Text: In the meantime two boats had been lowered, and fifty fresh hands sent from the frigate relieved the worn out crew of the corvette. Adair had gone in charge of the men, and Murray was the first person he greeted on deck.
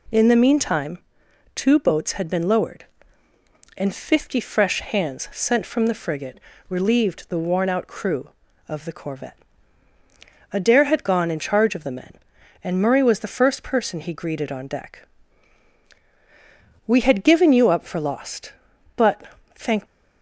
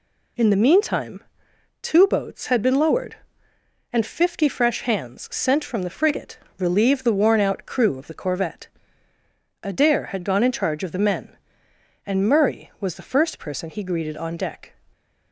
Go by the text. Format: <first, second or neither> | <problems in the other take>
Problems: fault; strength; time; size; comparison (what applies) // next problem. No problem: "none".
second | pauses between "meantime" and "two"; noticeable; at 0.9 s; 0.56 s long; noticeable in the second // pauses between "frigate" and "relieved"; slight; at 6.3 s; 0.30 s long; slight in the second // goes on to say "We had given you up for lost but thank"; strong; from 16.8 s on; 2.9 s long